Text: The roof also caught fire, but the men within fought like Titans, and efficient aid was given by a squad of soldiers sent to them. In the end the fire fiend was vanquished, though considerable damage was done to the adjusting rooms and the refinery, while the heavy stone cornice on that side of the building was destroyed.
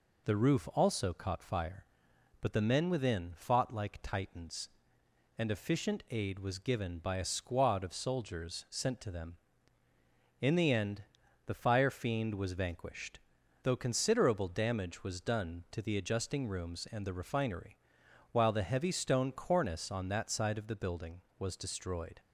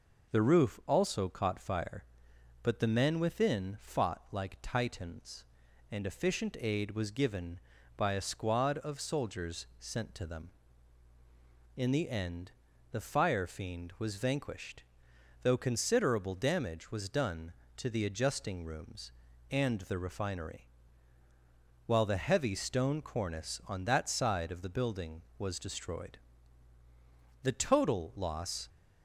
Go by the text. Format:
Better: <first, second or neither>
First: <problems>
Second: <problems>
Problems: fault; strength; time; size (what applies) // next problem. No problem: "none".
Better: first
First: pauses between "end" and "the"; at 11.0 s; 0.42 s long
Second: pauses between "end" and "the"; at 12.5 s; 0.38 s long // goes on to say "The total loss"; noticeable; from 27.4 s on; 1.2 s long